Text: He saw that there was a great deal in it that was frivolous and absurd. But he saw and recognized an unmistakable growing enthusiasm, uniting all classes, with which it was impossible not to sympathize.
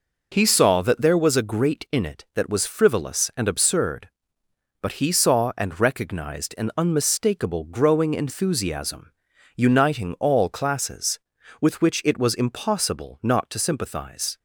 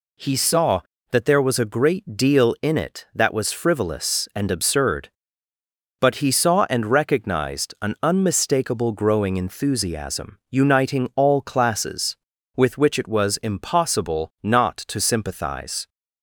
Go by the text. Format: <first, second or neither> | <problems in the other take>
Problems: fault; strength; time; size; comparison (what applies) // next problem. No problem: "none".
second | skips "deal"; at 1.8 s